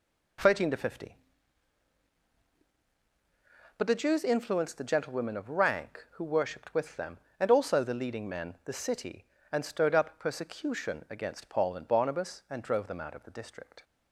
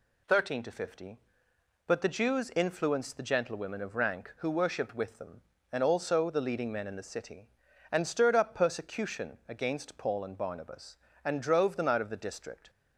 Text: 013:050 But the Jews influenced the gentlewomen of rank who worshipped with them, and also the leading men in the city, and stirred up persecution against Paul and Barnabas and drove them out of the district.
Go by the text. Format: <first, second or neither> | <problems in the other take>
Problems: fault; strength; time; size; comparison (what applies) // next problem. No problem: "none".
second | skips "in"; at 8.5 s